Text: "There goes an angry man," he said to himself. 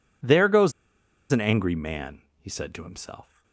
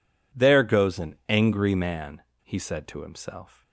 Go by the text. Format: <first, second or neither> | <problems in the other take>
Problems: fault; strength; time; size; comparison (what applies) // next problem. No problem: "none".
second | pauses between "goes" and "an"; noticeable; at 0.7 s; 0.60 s long